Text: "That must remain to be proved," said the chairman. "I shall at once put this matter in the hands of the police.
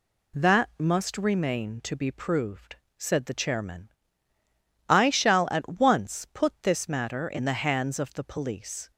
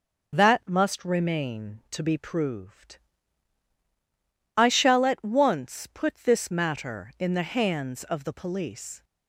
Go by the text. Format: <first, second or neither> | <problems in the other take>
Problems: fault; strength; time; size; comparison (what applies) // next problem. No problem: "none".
first | skips "said the chairman"; at 3.7 s